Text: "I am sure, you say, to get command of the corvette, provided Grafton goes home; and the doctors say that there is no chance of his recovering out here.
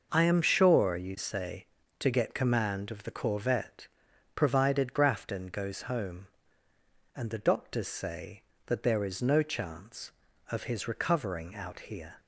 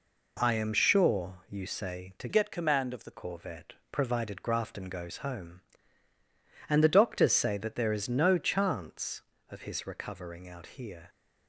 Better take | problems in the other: first | changes voice from "get" to "the"; from 2.2 to 3.1 s; 0.9 s long

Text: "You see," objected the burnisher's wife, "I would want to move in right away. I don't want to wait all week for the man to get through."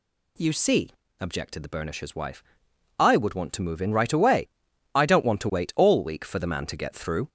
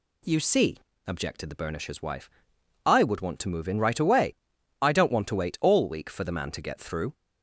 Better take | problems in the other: second | gets louder; slight; throughout; 2.5 dB

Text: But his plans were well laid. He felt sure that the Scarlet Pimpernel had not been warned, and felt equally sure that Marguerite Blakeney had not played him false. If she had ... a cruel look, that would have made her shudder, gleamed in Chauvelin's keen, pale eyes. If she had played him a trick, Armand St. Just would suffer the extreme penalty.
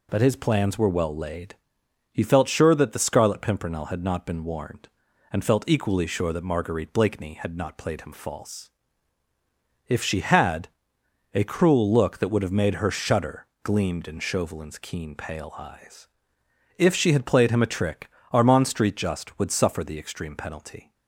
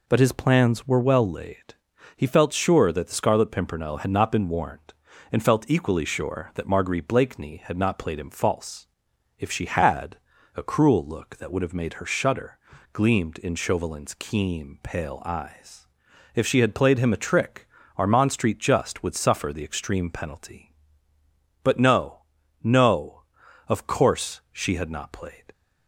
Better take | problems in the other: first | goes on to say "But no no of course she had not played"; strong; from 21.6 s on; 3.8 s long

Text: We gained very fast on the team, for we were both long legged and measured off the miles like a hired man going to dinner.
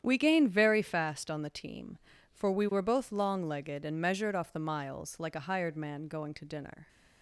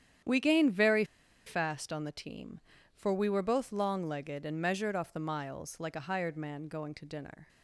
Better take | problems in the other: first | starts louder than the rest; strong; until 1.6 s; 9.5 dB; strong in the first // pauses between "very" and "fast"; at 1.0 s; 0.41 s long

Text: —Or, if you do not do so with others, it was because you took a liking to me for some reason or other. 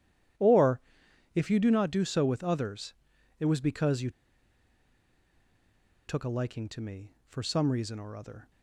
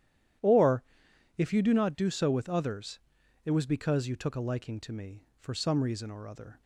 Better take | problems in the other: second | pauses between "you" and "took"; strong; at 4.0 s; 1.9 s long

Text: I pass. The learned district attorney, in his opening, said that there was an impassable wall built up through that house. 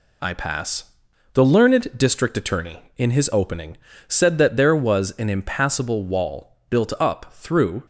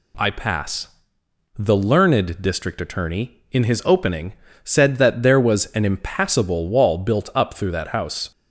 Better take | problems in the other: second | stops before "that house"; at 7.8 s

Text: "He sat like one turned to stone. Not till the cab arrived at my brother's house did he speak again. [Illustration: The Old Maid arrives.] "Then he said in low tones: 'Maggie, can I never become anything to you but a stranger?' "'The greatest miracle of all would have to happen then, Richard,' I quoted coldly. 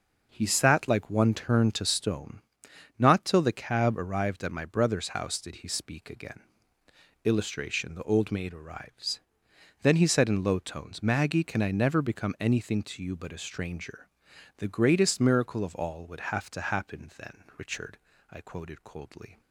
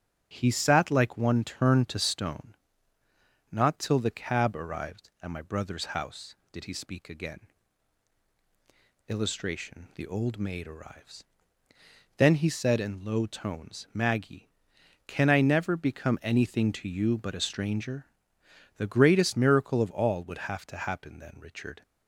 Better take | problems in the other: first | starts louder than the rest; strong; until 1.3 s; 10 dB // stops before "I quoted coldly"; at 21.8 s

